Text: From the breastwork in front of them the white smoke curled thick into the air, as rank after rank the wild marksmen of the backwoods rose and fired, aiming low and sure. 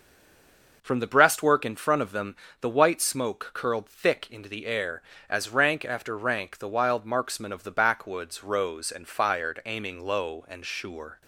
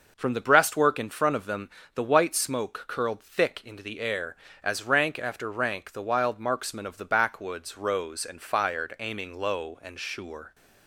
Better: second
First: stays silent before the first word; slight; until 0.8 s; 0.8 s long // pauses between "them" and "the"; slight; at 2.3 s; 0.26 s long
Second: pauses between "them" and "the"; slight; at 1.6 s; 0.26 s long

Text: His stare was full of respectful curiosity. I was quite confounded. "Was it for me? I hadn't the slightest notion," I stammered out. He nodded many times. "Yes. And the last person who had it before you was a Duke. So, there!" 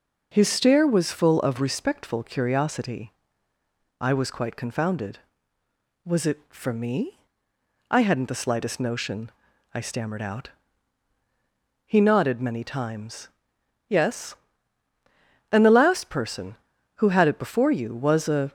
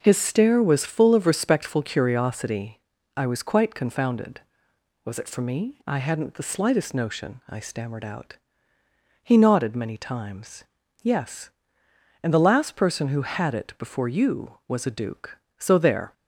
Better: second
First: stops before "Duke So there"; at 18.4 s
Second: none

